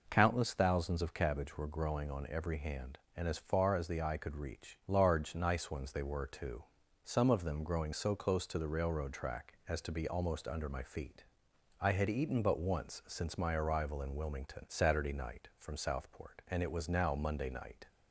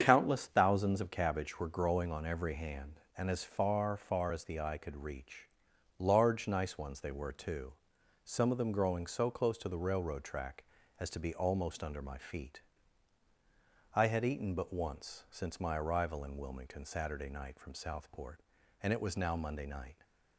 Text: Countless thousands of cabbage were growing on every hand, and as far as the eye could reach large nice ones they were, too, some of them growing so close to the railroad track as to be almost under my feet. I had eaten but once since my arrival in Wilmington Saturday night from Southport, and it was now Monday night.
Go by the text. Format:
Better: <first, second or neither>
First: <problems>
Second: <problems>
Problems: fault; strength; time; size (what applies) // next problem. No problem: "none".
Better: first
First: none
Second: starts louder than the rest; strong; until 1.0 s; 7.5 dB // says "far" twice; at 3.9 s // pauses between "reach" and "large"; noticeable; at 5.4 s; 0.52 s long